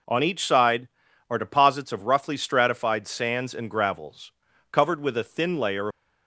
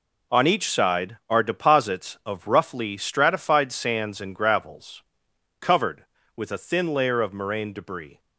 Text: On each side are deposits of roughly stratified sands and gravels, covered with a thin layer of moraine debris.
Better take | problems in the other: second | stops before "of moraine debris"; at 5.9 s

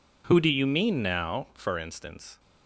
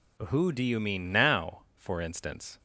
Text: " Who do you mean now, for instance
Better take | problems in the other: neither | none

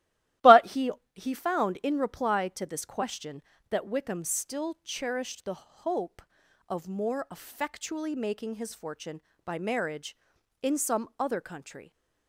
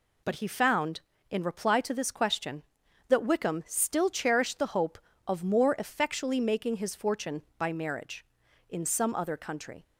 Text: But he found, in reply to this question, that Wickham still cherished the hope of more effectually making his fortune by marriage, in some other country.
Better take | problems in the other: second | starts louder than the rest; strong; until 1.6 s; 15 dB // says "he" twice; at 1.1 s

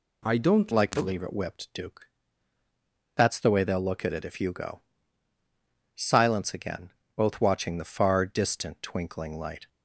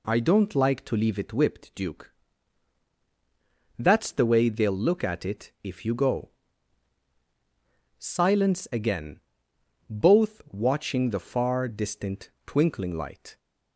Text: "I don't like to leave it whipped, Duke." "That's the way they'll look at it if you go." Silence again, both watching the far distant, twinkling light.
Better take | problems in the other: second | changes voice at "like"; from 0.7 s on; 8.9 s long

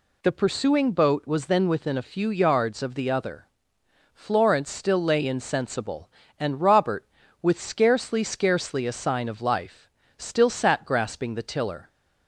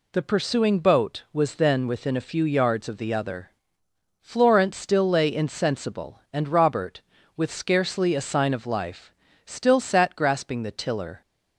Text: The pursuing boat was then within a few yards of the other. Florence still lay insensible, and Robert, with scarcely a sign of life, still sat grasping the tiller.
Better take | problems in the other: second | says "scarcely" twice; at 8.2 s

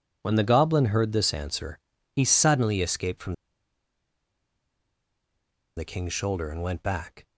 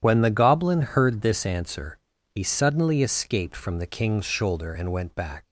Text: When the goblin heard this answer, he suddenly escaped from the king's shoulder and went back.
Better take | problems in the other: second | pauses between "from" and "the"; strong; at 3.3 s; 2.4 s long

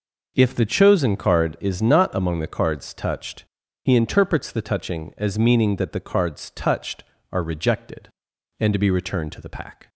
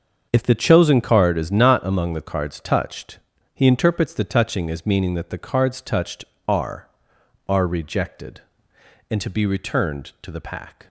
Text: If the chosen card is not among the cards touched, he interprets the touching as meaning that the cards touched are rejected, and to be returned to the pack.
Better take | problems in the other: first | starts louder than the rest; until 1.3 s; 7 dB // says "are" twice; at 7.4 s

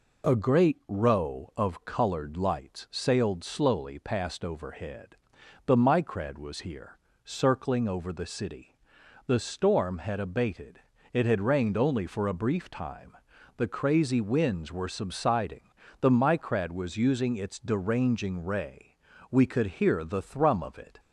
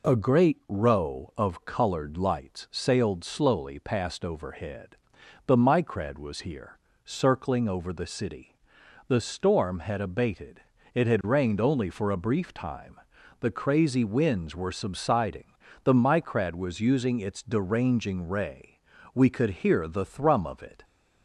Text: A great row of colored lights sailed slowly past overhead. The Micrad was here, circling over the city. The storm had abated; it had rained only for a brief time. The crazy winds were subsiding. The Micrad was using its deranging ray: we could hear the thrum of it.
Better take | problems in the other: neither | none

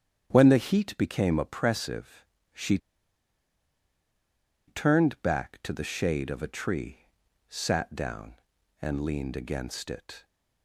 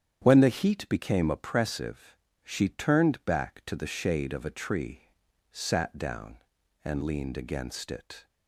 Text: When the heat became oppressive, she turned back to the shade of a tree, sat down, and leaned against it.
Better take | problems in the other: second | starts louder than the rest; strong; until 1.3 s; 9 dB; strong in the second // pauses between "she" and "turned"; strong; at 2.7 s; 1.9 s long

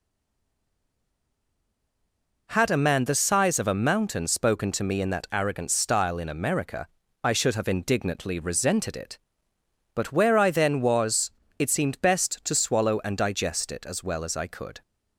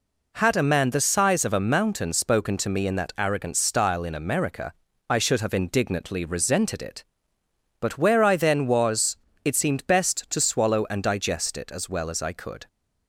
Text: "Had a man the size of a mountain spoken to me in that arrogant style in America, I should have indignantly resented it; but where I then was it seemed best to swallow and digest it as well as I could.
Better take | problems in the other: second | stays silent before the first word; until 2.4 s; 2.4 s long // pauses between "was" and "it"; slight; at 11.3 s; 0.26 s long; slight in the second

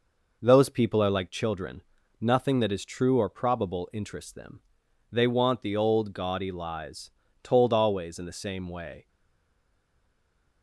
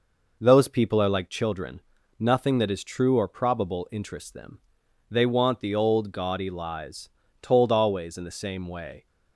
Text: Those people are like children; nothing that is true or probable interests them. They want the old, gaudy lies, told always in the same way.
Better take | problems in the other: second | stays silent after the last word; noticeable; from 9.0 s on; 1.6 s long

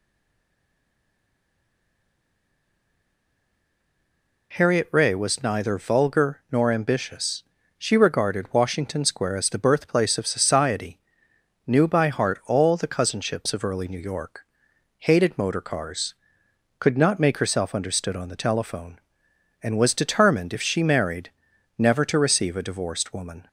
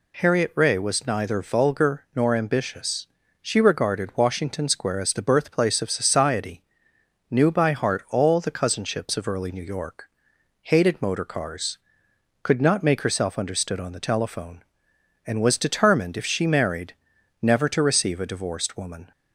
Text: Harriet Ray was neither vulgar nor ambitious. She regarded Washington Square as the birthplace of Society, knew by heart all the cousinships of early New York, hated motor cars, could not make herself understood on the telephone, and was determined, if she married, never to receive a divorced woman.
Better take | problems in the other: second | stays silent before the first word; strong; until 4.5 s; 4.5 s long

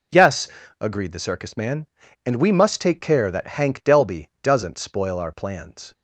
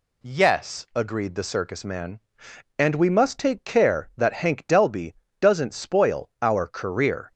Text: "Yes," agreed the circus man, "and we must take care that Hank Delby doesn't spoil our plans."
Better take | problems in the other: first | pauses between "Delby" and "doesn't"; slight; at 5.1 s; 0.24 s long // says "career" for "plans"; at 6.6 s

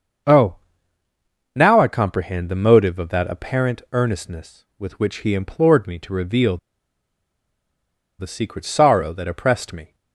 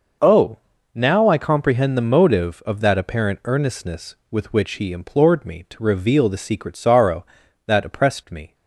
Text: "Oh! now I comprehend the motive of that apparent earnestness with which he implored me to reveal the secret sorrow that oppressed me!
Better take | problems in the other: second | starts louder than the rest; until 2.2 s; 6.5 dB // pauses between "reveal" and "the"; strong; at 6.5 s; 1.6 s long

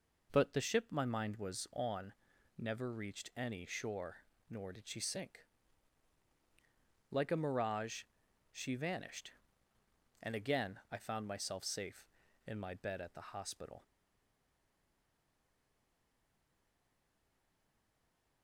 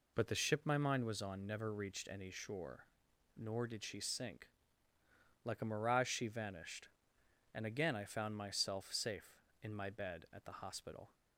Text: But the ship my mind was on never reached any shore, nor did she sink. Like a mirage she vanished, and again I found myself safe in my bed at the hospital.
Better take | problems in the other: second | pauses between "on" and "never"; at 2.1 s; 0.44 s long // pauses between "mirage" and "she"; noticeable; at 8.0 s; 0.50 s long // stays silent after the last word; strong; from 13.8 s on; 4.6 s long

